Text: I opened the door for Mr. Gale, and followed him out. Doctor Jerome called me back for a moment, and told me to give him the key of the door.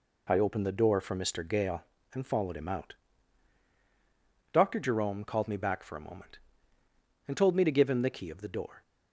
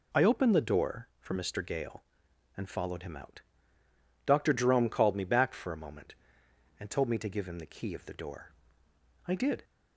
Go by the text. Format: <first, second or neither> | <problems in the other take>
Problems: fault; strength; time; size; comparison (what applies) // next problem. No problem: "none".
first | goes on to say "I did"; slight; from 9.2 s on; 0.38 s long